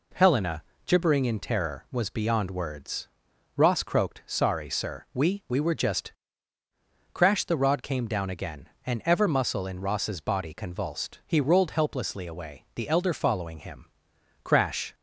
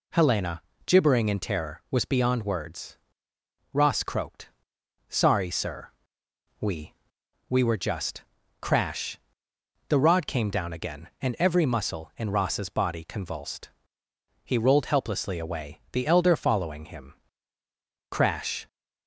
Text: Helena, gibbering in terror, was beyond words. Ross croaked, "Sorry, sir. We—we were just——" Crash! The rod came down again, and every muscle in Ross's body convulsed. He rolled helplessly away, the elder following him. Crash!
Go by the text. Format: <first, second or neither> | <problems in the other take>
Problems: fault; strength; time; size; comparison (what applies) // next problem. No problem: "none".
second | says "ever" for "every"; at 9.0 s